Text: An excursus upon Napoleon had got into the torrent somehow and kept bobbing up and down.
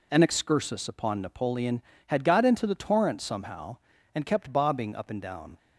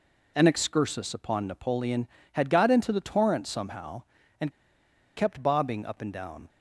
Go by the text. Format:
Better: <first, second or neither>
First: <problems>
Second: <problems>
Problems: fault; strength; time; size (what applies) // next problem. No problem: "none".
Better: first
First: none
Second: pauses between "and" and "kept"; noticeable; at 4.4 s; 0.66 s long